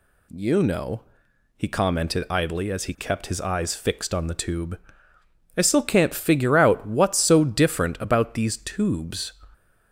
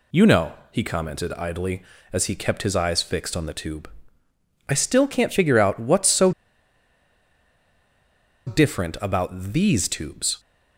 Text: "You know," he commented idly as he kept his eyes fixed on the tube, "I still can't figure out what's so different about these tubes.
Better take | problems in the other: first | pauses between "so" and "different"; strong; at 6.3 s; 2.1 s long

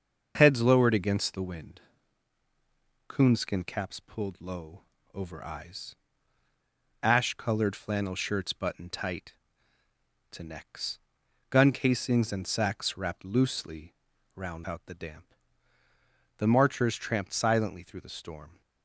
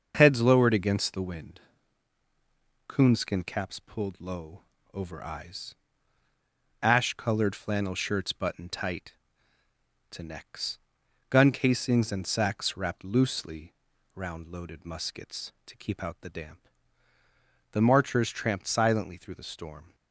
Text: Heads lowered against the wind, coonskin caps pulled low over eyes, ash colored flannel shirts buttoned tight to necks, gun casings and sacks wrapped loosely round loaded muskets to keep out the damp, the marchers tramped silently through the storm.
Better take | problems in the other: second | starts louder than the rest; until 1.3 s; 6.5 dB; also in the second // pauses between "low" and "over"; slight; at 4.8 s; 0.32 s long; slight in the second // pauses between "loosely" and "round"; at 13.9 s; 0.40 s long; also in the second // skips "loaded muskets to keep"; at 14.6 s

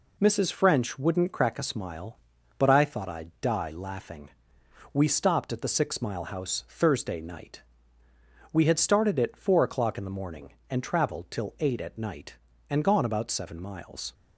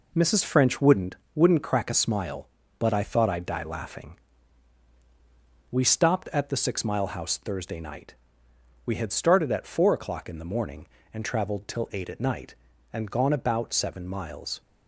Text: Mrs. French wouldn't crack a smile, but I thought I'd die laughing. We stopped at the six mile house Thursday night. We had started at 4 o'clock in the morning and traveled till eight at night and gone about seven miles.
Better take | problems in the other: first | says "wouldn't" twice; at 1.3 s

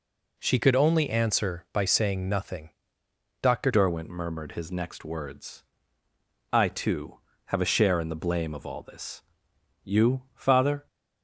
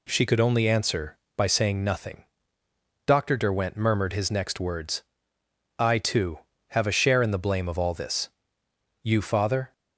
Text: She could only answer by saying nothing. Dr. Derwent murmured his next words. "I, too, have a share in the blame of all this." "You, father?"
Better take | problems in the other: second | changes voice at "Derwent"; from 3.6 s on; 7.2 s long

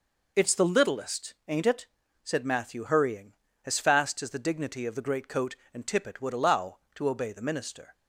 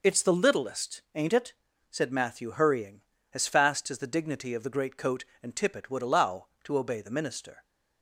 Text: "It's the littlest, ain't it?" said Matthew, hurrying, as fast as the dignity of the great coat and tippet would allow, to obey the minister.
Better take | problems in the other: neither | none

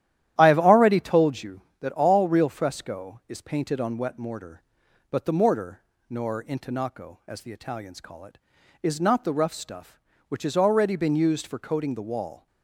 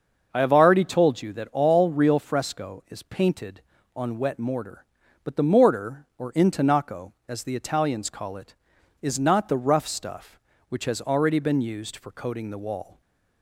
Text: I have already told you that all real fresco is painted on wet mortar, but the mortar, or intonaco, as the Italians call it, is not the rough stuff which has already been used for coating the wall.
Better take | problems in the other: second | starts louder than the rest; strong; until 1.3 s; 12 dB; also in the second // says "nor" for "or"; at 6.1 s

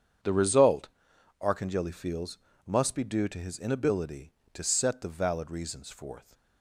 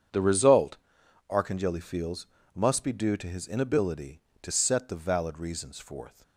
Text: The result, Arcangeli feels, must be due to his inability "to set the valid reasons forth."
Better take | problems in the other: neither | starts louder than the rest; strong; the same in both

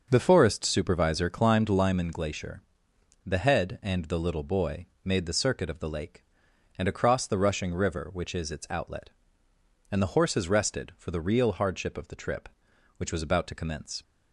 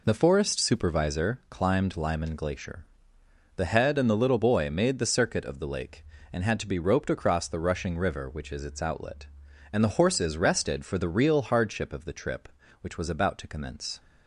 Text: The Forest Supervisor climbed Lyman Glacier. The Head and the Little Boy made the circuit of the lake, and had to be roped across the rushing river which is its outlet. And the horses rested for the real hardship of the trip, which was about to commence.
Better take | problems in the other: second | starts louder than the rest; noticeable; until 1.1 s; 6 dB // pauses between "Boy" and "made"; slight; at 4.8 s; 0.18 s long // skips "had to be roped"; at 6.8 s

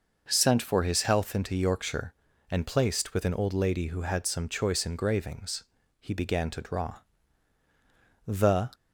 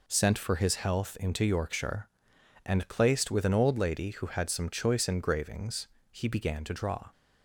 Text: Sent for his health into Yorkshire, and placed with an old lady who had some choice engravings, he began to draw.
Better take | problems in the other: second | goes on to say "The"; slight; from 8.2 s on; 0.42 s long

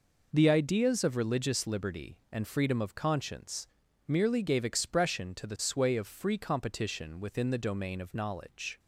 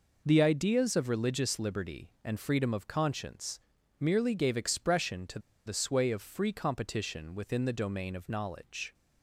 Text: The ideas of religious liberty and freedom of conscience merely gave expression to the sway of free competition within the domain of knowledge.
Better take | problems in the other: first | pauses between "conscience" and "merely"; at 3.5 s; 0.40 s long; also in the first // pauses between "to" and "the"; slight; at 5.3 s; 0.27 s long

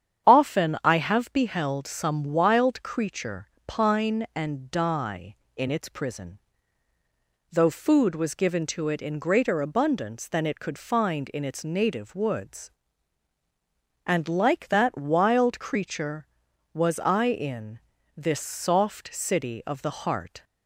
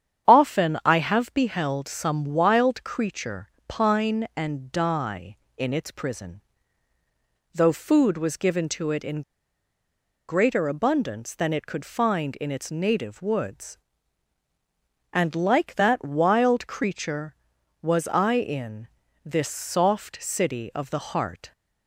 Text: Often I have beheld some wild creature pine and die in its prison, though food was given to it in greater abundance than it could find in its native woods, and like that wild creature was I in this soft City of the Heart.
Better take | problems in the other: first | starts louder than the rest; strong; until 1.3 s; 8.5 dB; strong in the first // pauses between "creature" and "pine"; slight; at 3.4 s; 0.18 s long; slight in the first // pauses between "in" and "greater"; at 9.2 s; 1.0 s long // pauses between "in" and "this"; slight; at 18.8 s; 0.36 s long; slight in the first

